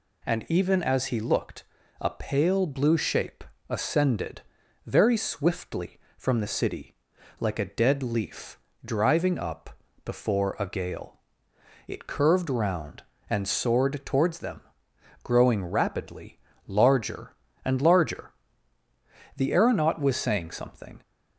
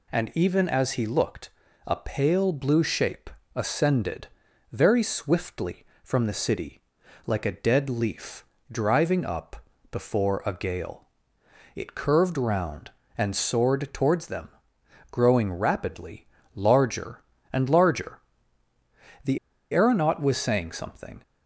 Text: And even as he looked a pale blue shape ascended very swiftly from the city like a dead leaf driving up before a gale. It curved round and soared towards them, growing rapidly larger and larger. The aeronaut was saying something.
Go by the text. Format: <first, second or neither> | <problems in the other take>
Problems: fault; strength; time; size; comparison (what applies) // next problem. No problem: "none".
first | pauses between "looked" and "a"; at 1.4 s; 0.38 s long; also in the first // pauses between "shape" and "ascended"; slight; at 3.2 s; 0.26 s long; slight in the first // pauses between "ascended" and "very"; at 4.2 s; 0.44 s long; also in the first // pauses between "city" and "like"; at 6.8 s; 0.44 s long; also in the first // pauses between "leaf" and "driving"; slight; at 8.4 s; 0.26 s long; slight in the first // pauses between "up" and "before"; slight; at 9.6 s; 0.28 s long; slight in the first // pauses between "rapidly" and "larger"; slight; at 16.2 s; 0.28 s long; slight in the first // pauses between "The" and "aeronaut"; slight; at 19.3 s; 0.35 s long